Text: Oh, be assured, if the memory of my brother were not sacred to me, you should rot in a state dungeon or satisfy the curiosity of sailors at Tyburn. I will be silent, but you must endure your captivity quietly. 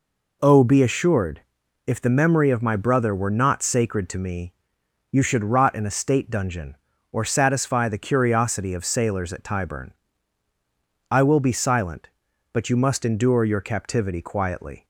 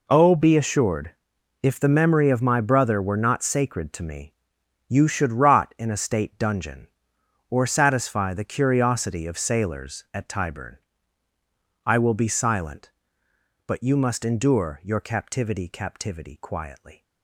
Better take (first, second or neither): first